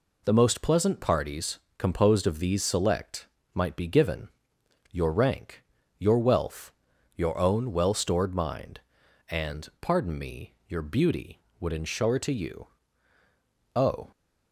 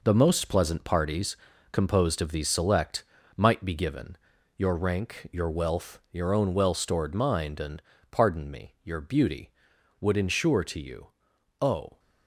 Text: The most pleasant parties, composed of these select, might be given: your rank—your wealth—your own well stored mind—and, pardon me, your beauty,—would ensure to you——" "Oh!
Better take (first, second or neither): first